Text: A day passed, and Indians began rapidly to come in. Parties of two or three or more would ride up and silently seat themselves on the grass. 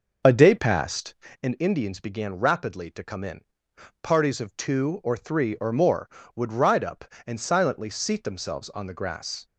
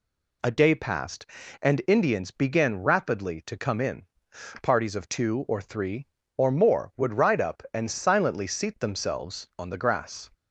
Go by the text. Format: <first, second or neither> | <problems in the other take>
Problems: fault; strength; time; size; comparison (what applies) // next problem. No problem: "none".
second | starts louder than the rest; noticeable; until 1.3 s; 6 dB